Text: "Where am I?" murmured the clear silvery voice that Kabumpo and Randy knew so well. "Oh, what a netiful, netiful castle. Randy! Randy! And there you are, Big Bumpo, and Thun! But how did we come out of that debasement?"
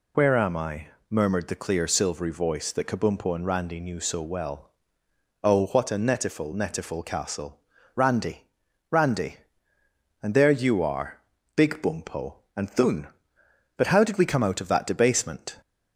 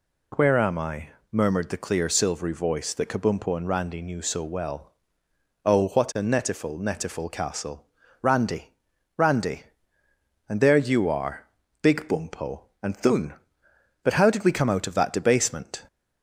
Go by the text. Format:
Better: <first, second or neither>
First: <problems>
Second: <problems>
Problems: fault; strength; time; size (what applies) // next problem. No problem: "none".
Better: second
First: loses the start of "Where"; at 0.1 s; 45 ms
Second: none